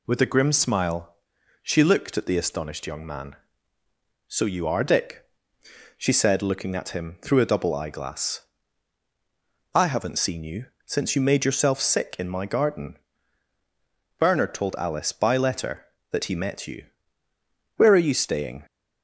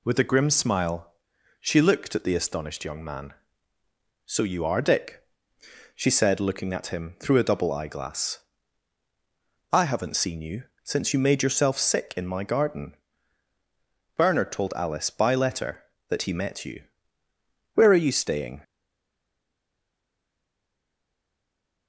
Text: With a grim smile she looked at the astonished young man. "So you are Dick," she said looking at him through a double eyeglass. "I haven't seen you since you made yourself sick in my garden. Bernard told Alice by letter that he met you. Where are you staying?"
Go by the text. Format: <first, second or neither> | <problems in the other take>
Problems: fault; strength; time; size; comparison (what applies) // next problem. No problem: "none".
first | pauses between "smile" and "she"; noticeable; at 1.1 s; 0.48 s long; noticeable in the first // pauses between "you" and "since"; slight; at 10.6 s; 0.18 s long; slight in the first // stays silent after the last word; strong; from 18.6 s on; 3.2 s long